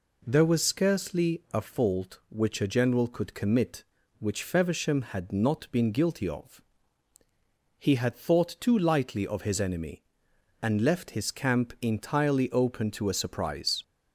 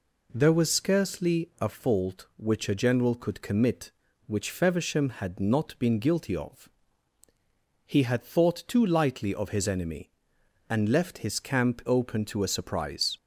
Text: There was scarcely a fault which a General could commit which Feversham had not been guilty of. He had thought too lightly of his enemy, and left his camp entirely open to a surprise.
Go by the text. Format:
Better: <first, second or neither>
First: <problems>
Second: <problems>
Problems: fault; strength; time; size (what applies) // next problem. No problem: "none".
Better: first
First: none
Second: skips "entirely"; at 11.8 s